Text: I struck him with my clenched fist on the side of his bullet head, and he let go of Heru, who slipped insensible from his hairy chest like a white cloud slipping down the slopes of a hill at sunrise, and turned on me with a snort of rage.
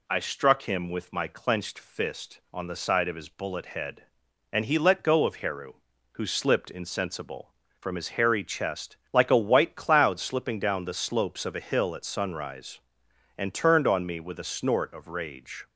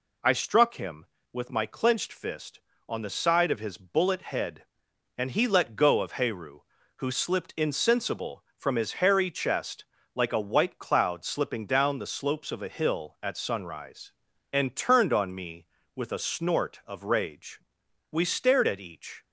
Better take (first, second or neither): first